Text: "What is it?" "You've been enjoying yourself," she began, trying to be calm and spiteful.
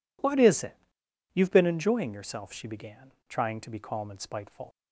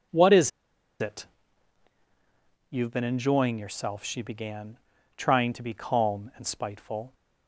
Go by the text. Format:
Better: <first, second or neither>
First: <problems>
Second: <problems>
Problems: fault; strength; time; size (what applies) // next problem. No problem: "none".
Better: first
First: none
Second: pauses between "is" and "it"; noticeable; at 0.5 s; 0.52 s long